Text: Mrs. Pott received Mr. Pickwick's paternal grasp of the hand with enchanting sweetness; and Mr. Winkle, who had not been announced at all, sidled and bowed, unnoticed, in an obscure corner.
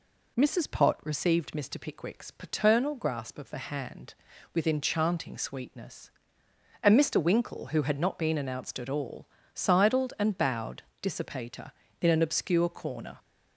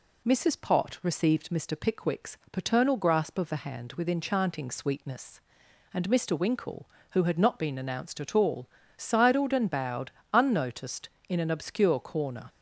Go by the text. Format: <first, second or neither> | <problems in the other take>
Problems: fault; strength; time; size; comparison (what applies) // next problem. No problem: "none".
second | says "dissipator" for "unnoticed"; at 11.0 s